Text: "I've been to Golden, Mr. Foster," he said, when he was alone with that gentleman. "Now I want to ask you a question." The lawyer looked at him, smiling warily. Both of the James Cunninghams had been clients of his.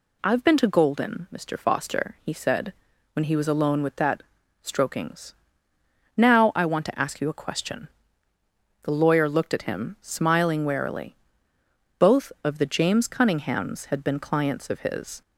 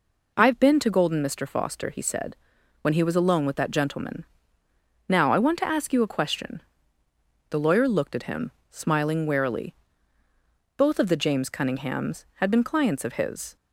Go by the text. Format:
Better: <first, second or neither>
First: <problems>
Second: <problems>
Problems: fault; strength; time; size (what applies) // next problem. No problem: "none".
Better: second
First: says "strokings" for "gentleman"; at 4.6 s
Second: none